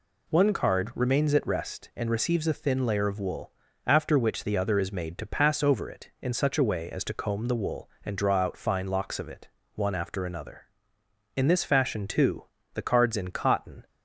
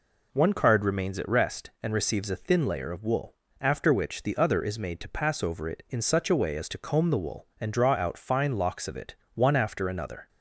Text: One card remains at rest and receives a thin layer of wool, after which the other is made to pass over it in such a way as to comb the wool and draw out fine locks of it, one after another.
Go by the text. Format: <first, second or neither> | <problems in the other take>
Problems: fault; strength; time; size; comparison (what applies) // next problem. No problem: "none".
second | goes on to say "In this fashion too the cards in cotton"; strong; from 11.3 s on; 2.5 s long